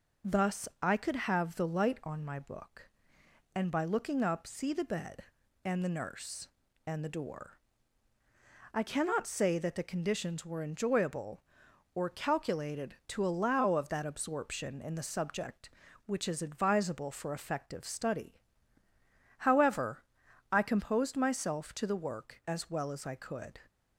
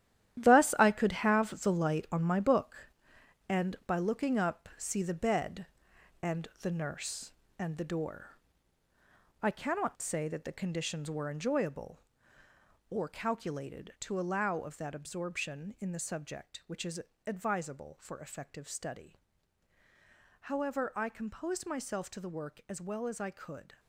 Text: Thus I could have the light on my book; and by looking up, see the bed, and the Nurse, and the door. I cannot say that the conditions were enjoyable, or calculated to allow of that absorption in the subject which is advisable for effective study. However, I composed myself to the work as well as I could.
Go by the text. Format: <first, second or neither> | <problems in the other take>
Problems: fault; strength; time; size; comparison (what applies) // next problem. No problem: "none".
first | gets quieter; strong; throughout; 10 dB // pauses between "and" and "the"; slight; at 6.4 s; 0.16 s long // pauses between "is" and "advisable"; slight; at 17.0 s; 0.24 s long